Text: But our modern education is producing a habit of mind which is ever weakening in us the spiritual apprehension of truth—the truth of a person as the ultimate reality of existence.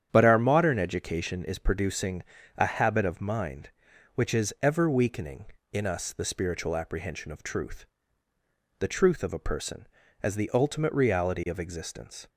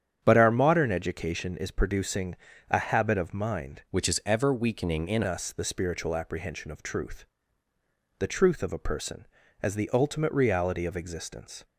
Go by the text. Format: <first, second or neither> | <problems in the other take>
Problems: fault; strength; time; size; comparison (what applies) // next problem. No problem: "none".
first | starts louder than the rest; strong; until 1.2 s; 8.5 dB; strong in the first // pauses between "producing" and "a"; slight; at 2.3 s; 0.34 s long; slight in the first // changes voice from "which" to "in"; from 3.9 to 5.2 s; 1.3 s long